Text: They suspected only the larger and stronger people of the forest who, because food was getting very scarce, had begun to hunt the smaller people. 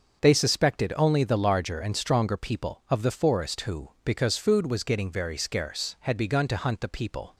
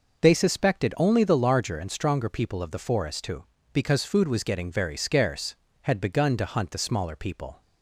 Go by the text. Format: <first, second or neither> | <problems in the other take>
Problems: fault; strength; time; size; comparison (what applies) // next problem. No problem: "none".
second | starts louder than the rest; until 1.2 s; 6.5 dB // skips "smaller"; at 6.8 s